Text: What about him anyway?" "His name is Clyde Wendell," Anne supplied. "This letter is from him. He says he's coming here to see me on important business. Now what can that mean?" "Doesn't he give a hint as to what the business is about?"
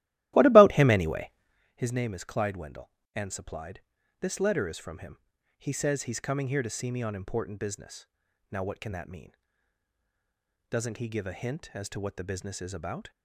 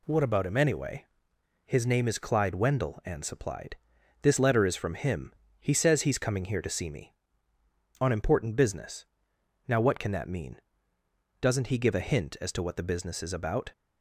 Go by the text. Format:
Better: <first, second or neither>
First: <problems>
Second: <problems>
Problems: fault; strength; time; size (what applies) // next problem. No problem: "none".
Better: second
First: starts louder than the rest; strong; until 1.8 s; 15 dB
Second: none